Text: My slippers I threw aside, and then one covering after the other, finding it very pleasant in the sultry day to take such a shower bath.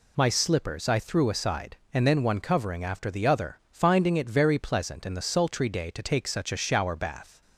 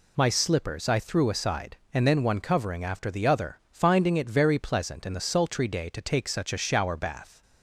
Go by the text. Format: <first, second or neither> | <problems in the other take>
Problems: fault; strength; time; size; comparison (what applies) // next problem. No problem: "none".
neither | none